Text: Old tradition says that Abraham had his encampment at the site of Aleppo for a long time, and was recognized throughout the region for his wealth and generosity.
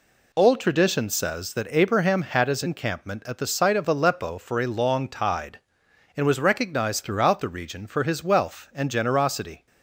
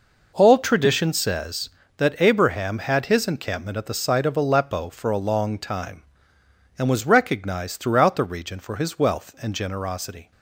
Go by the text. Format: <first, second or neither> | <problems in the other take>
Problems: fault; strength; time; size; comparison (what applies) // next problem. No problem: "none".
second | says "tide" for "time"; at 5.0 s